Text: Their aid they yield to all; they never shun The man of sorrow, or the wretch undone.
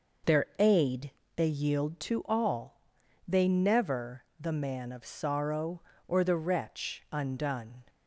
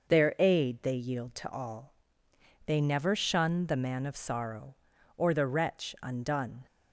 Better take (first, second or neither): second